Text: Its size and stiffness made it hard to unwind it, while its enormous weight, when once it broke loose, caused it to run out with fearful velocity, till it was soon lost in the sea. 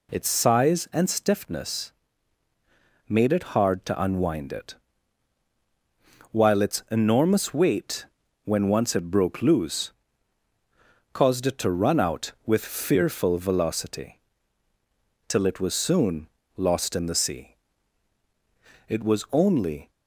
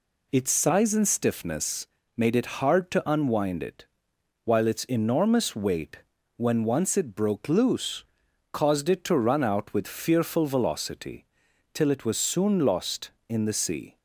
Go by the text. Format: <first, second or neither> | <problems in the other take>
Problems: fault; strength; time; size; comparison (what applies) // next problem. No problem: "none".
second | pauses between "stiffness" and "made"; at 1.9 s; 1.1 s long; slight in the second // pauses between "soon" and "lost"; slight; at 16.2 s; 0.28 s long // goes on to say "It was only"; noticeable; from 18.8 s on; 1.0 s long